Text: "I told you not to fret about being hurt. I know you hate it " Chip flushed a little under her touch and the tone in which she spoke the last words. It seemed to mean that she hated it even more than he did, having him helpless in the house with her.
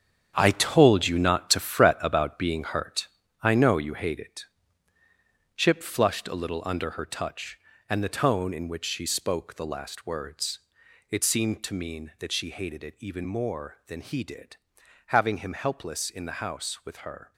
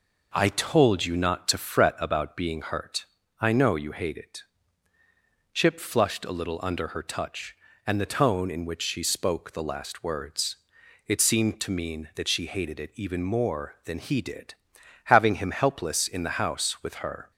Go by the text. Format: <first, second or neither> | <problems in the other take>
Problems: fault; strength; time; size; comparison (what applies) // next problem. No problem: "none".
second | gets quieter; strong; throughout; 8 dB